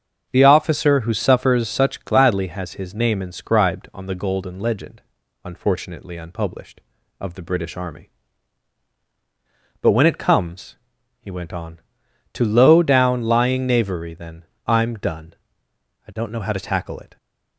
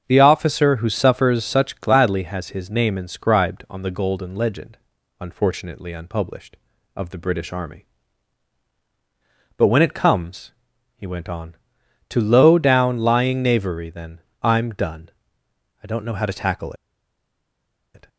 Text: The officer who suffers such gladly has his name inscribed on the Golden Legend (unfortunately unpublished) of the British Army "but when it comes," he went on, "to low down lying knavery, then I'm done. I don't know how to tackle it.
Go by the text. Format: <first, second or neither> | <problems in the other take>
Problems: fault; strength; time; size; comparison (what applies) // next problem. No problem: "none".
first | starts louder than the rest; strong; until 1.0 s; 7.5 dB; strong in the first // pauses between "then" and "I'm"; slight; at 14.1 s; 0.22 s long; slight in the first // pauses between "tackle" and "it"; at 16.7 s; 1.2 s long